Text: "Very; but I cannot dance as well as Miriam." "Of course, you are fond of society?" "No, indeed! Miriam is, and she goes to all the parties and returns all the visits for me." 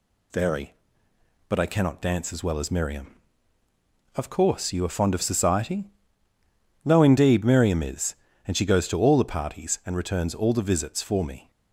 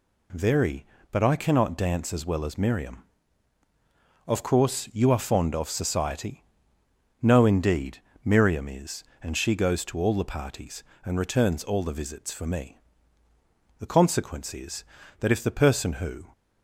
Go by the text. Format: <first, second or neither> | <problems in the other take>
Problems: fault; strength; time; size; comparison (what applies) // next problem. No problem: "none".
first | goes on to say "The consequence is that if the person who"; strong; from 13.7 s on; 2.4 s long